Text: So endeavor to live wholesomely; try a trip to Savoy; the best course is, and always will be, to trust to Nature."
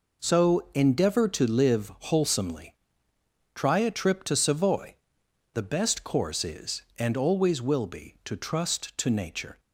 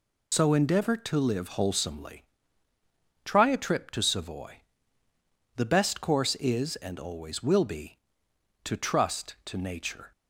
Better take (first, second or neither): first